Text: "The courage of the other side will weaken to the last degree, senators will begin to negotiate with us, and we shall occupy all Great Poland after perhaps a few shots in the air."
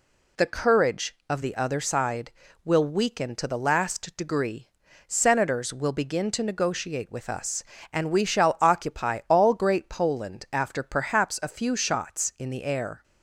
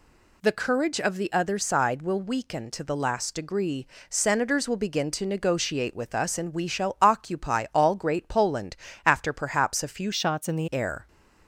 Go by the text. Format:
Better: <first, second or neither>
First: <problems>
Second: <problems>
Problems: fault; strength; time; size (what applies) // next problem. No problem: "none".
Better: first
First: none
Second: pauses between "Poland" and "after"; slight; at 8.7 s; 0.30 s long // changes voice from "shots" to "the"; from 10.1 to 10.6 s; 0.5 s long